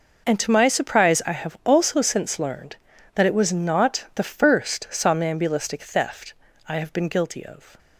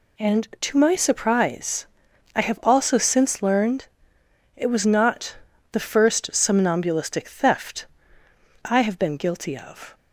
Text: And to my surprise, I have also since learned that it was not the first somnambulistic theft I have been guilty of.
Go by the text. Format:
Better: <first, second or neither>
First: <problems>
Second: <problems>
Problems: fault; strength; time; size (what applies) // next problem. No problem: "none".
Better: first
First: pauses between "theft" and "I"; slight; at 6.3 s; 0.34 s long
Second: skips "that"; at 4.2 s // pauses between "not" and "the"; slight; at 5.3 s; 0.36 s long // pauses between "theft" and "I"; noticeable; at 7.8 s; 0.78 s long